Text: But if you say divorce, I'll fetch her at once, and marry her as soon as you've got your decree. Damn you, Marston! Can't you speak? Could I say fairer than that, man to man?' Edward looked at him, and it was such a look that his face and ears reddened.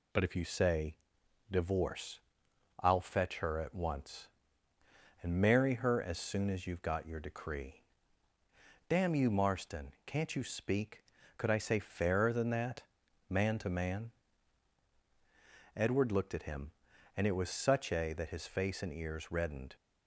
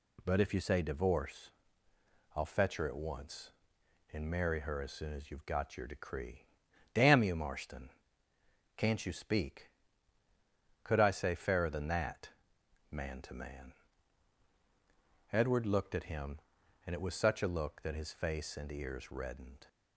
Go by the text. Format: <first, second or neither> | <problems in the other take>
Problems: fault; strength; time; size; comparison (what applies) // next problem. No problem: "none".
second | pauses between "say" and "divorce"; noticeable; at 0.9 s; 0.54 s long // skips "look"; at 18.1 s